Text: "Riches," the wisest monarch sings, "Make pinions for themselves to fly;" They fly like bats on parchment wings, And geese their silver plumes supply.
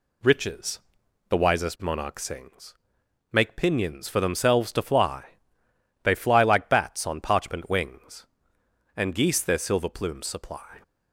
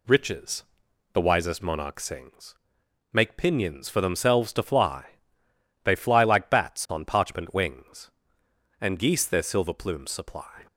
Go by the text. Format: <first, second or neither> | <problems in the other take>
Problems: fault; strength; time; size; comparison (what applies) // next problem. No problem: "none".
neither | none